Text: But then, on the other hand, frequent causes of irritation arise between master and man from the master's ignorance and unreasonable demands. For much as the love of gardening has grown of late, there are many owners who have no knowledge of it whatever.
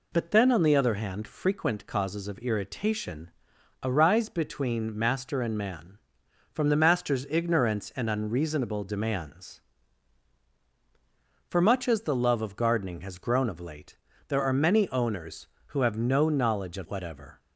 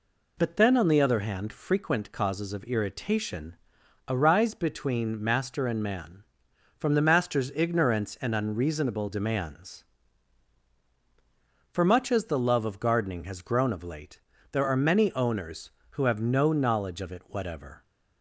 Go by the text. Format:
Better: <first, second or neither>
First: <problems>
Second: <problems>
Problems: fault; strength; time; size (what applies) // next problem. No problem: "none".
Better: second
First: pauses between "irritation" and "arise"; noticeable; at 3.3 s; 0.52 s long // skips "it"; at 16.8 s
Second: pauses between "irritation" and "arise"; noticeable; at 3.5 s; 0.52 s long